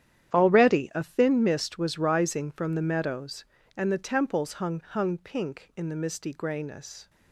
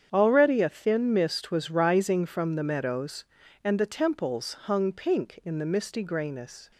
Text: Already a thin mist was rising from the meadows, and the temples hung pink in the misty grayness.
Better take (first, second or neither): second